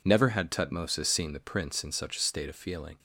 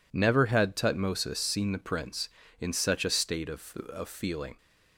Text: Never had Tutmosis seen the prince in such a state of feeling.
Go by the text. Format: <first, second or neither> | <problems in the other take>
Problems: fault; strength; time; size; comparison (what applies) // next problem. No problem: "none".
first | says "of" twice; at 3.9 s